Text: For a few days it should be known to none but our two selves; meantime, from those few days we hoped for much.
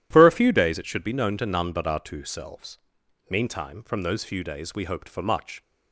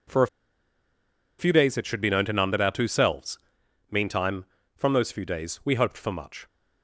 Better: first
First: none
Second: pauses between "a" and "few"; at 0.2 s; 1.1 s long

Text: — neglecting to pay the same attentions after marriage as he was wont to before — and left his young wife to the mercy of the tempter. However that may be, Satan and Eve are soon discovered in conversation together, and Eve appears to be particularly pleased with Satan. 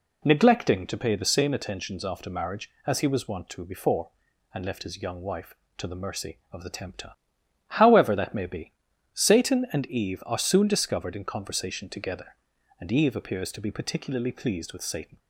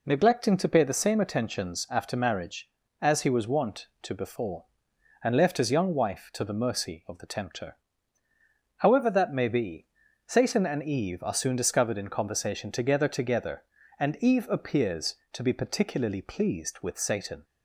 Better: first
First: none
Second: says "together" twice; at 13.0 s

